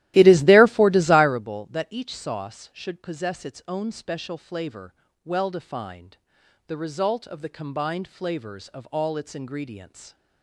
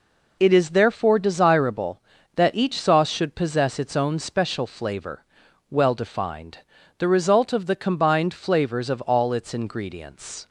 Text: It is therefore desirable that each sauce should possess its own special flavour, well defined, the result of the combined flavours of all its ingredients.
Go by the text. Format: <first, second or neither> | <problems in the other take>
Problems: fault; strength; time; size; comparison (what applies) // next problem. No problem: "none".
second | starts louder than the rest; strong; until 1.5 s; 15 dB